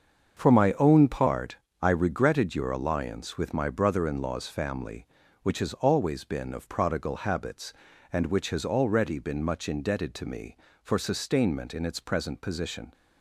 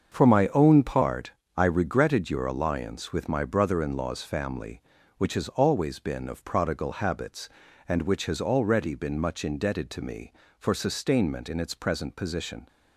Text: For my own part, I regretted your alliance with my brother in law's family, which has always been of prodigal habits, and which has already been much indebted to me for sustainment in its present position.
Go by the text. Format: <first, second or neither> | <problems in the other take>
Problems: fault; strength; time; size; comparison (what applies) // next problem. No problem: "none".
neither | starts louder than the rest; the same in both